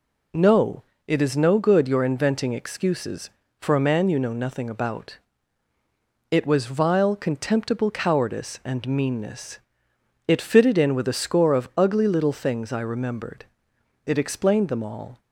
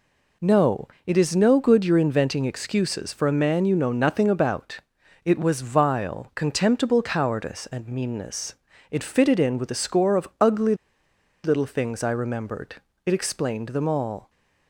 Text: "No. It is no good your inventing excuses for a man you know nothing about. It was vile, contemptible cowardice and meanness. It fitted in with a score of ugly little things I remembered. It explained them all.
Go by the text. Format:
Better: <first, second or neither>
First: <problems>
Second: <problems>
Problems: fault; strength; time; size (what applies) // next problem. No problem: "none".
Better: first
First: none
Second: pauses between "ugly" and "little"; noticeable; at 10.7 s; 0.69 s long